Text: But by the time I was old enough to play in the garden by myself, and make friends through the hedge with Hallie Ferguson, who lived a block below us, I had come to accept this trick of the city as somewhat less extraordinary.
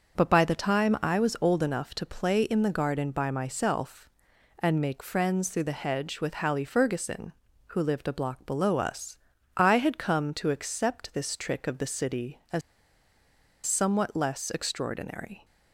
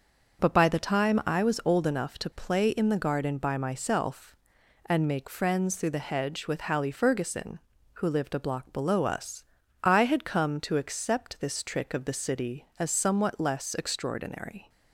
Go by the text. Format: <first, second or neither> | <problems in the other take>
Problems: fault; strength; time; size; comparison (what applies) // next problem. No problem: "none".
second | starts louder than the rest; until 1.2 s; 6.5 dB; also in the second // pauses between "as" and "somewhat"; at 12.6 s; 1.0 s long